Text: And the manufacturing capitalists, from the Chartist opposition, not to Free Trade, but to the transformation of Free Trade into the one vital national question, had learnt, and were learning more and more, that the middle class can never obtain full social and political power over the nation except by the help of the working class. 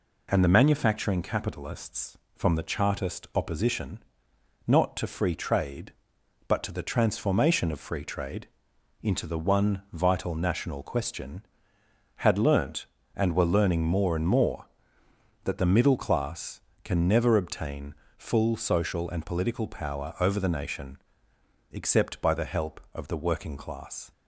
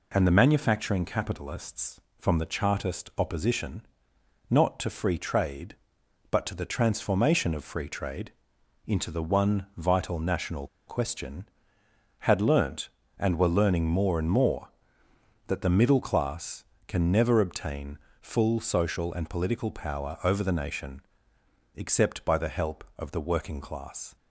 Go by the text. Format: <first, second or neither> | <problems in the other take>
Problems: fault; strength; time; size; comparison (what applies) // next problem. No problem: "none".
first | pauses between "Trade" and "into"; noticeable; at 8.3 s; 0.56 s long; noticeable in the first // pauses between "national" and "question"; slight; at 10.6 s; 0.20 s long // pauses between "obtain" and "full"; slight; at 17.9 s; 0.24 s long; slight in the first // pauses between "nation" and "except"; noticeable; at 21.0 s; 0.74 s long; noticeable in the first